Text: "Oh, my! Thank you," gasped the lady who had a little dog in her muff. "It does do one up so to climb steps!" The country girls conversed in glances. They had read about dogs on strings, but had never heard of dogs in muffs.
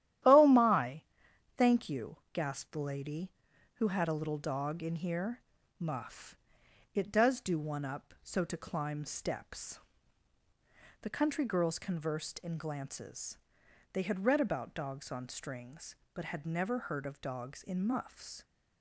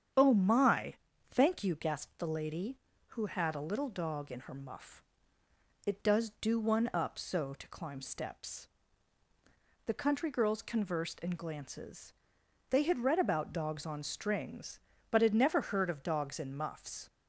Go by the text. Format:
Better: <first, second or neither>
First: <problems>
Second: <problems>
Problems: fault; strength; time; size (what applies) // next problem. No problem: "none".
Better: second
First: starts louder than the rest; strong; until 1.8 s; 12 dB // says "here" for "her"; at 4.9 s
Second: starts louder than the rest; strong; until 1.5 s; 8.5 dB